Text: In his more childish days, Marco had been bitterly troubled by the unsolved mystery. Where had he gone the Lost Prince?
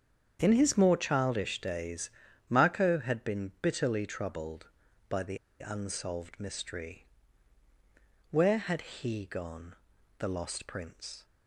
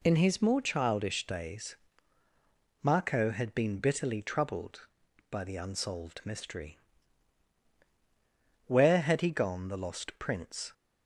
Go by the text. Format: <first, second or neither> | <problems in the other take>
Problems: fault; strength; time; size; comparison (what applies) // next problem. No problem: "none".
second | starts louder than the rest; strong; until 1.4 s; 8 dB // pauses between "the" and "unsolved"; slight; at 5.3 s; 0.23 s long // pauses between "gone" and "the"; at 9.7 s; 0.44 s long